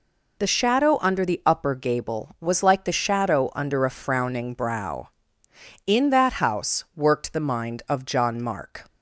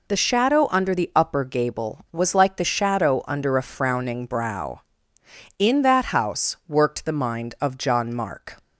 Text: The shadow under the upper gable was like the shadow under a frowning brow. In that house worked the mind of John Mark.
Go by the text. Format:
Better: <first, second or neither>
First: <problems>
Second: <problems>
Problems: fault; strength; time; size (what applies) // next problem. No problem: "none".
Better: neither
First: none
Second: none